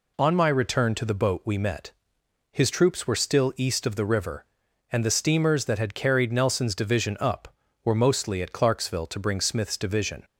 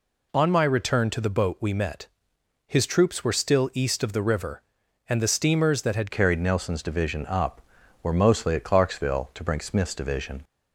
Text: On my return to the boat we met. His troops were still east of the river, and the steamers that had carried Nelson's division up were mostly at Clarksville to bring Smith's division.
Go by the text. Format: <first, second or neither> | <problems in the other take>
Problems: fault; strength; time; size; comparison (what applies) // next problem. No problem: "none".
first | changes voice at "carried"; from 6.1 s on; 4.3 s long